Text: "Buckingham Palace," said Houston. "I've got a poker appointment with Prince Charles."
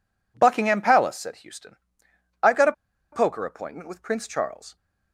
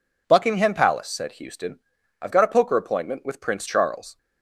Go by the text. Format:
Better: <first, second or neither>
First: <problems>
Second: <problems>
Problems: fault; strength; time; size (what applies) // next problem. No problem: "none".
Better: second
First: pauses between "a" and "poker"; at 2.7 s; 0.40 s long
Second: none